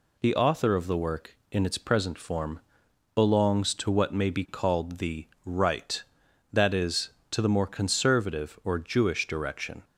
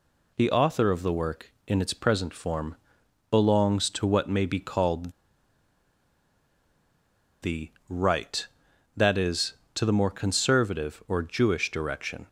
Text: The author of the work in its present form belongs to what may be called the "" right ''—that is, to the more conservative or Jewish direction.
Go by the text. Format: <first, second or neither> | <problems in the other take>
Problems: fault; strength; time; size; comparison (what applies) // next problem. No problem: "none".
first | pauses between "form" and "belongs"; noticeable; at 2.7 s; 0.54 s long; noticeable in the first // pauses between "called" and "the"; strong; at 5.1 s; 2.3 s long